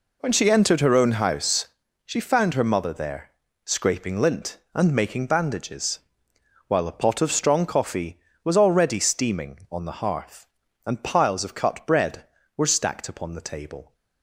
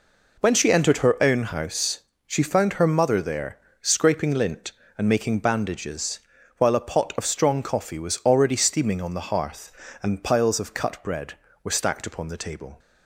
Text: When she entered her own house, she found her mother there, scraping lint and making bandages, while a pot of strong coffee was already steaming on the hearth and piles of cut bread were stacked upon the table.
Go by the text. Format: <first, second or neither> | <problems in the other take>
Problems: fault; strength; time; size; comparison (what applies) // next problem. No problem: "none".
neither | none